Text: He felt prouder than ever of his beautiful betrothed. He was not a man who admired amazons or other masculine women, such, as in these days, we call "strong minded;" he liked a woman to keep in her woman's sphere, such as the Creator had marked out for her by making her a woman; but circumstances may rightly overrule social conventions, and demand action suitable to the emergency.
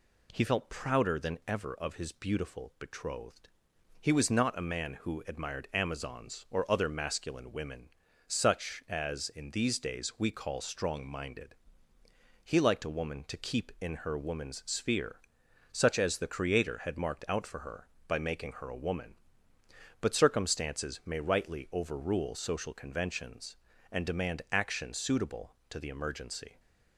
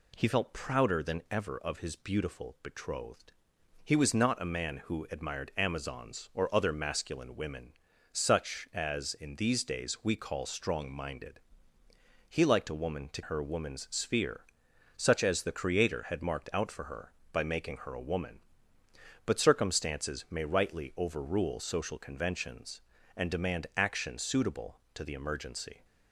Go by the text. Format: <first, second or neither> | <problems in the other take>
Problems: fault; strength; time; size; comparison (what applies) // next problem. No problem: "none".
first | skips "keep in"; at 13.2 s